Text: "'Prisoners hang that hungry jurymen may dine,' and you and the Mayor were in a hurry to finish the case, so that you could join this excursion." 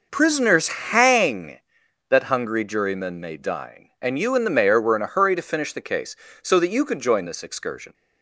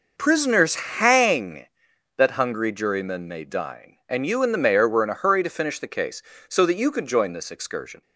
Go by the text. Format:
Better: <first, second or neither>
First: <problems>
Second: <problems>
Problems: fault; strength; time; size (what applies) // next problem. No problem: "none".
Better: neither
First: none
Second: none